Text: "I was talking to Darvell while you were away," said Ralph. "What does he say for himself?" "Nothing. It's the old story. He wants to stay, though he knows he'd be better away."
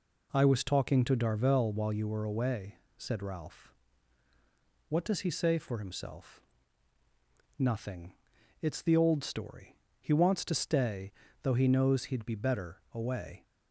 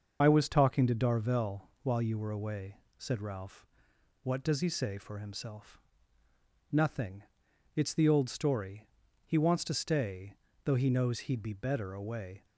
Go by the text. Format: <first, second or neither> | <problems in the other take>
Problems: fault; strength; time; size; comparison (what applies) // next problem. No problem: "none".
first | loses the start of "I"; at 0.2 s; 40 ms // starts louder than the rest; until 1.2 s; 6.5 dB